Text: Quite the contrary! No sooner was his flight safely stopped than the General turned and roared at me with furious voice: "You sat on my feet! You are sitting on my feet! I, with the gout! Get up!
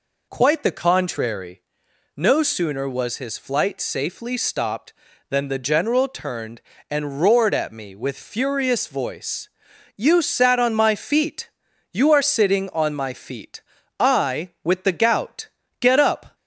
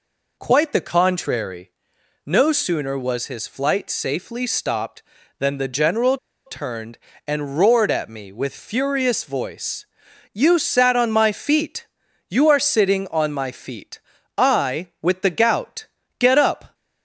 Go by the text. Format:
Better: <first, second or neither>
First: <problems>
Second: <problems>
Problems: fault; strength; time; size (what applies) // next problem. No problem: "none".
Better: first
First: none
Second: pauses between "General" and "turned"; slight; at 6.1 s; 0.30 s long